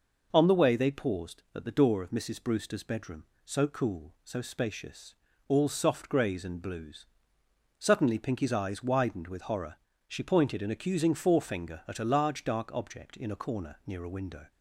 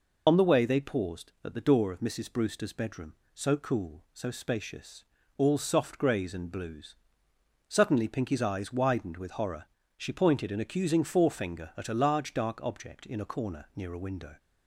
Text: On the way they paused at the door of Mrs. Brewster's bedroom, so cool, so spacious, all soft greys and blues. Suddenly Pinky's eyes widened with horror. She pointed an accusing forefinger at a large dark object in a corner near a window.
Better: first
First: none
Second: loses the start of "On"; at 0.2 s; 50 ms

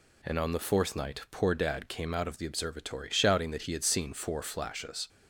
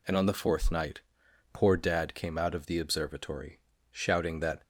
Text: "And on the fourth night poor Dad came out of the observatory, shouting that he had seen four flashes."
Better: first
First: none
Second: pauses between "night" and "poor"; noticeable; at 0.9 s; 0.52 s long // stops before "he had seen four flashes"; at 4.6 s

